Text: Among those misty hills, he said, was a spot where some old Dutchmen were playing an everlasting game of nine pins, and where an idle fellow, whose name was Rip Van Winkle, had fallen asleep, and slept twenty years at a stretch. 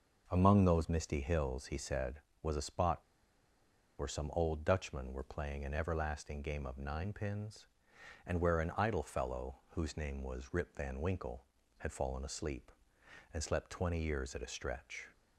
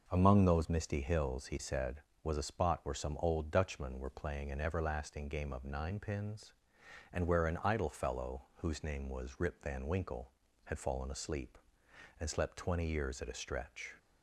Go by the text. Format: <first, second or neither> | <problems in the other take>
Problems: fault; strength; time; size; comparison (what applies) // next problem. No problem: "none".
second | pauses between "spot" and "where"; at 2.9 s; 1.0 s long